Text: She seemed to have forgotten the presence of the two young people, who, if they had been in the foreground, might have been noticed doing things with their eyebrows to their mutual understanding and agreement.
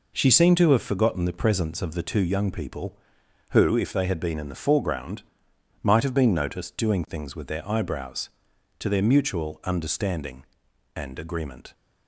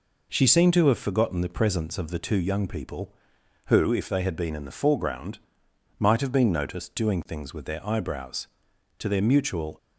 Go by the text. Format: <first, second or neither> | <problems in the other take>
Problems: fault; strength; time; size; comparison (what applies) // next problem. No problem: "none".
first | stops before "understanding and agreement"; at 9.7 s